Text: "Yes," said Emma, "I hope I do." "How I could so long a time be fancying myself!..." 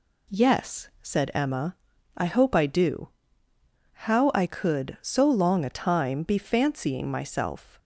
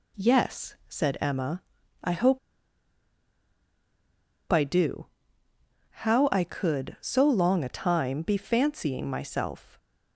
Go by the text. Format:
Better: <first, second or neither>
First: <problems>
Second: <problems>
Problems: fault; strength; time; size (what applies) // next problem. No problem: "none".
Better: first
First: none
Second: pauses between "hope" and "I"; strong; at 2.3 s; 2.1 s long